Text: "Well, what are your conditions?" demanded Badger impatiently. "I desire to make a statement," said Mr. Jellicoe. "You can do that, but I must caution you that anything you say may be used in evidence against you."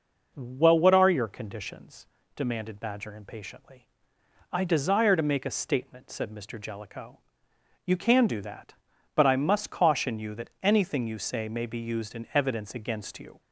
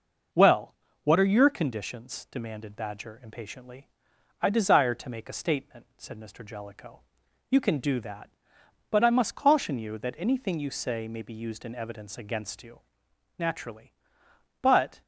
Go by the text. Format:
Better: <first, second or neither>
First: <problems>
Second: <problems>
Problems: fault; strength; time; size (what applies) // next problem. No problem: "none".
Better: first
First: none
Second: goes on to say "Naturally But"; from 13.3 s on; 1.6 s long